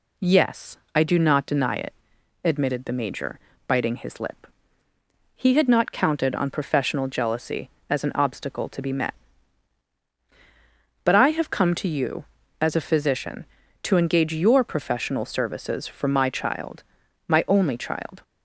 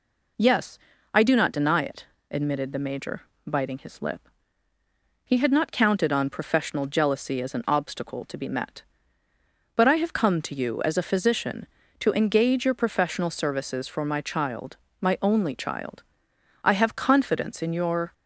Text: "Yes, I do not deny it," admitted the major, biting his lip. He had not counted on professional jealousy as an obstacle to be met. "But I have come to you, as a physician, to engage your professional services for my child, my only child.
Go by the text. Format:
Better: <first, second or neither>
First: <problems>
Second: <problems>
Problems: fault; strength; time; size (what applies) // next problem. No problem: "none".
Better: first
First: none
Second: goes on to say "I have confidence in your"; from 16.6 s on; 1.4 s long